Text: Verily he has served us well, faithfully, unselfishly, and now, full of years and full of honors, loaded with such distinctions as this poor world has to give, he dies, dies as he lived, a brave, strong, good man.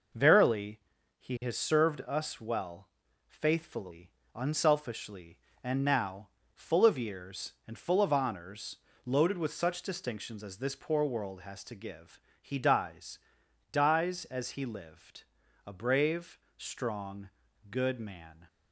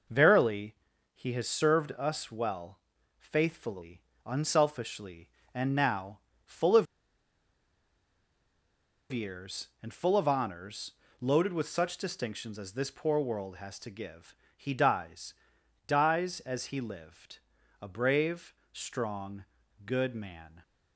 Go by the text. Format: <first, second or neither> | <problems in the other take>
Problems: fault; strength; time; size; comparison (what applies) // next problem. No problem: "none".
first | pauses between "Verily" and "he"; at 0.7 s; 0.38 s long; also in the first // pauses between "of" and "years"; strong; at 6.8 s; 2.2 s long